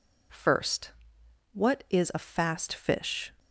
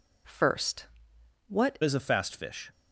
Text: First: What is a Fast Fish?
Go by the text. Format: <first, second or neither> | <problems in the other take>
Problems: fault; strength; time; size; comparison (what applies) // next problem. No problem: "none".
first | changes voice at "is"; from 1.8 s on; 0.9 s long